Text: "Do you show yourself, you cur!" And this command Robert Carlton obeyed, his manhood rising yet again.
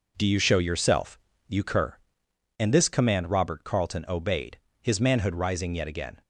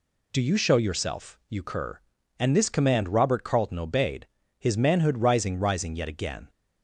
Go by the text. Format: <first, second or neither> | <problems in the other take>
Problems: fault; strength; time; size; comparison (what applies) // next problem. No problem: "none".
first | says "rising" twice; at 5.5 s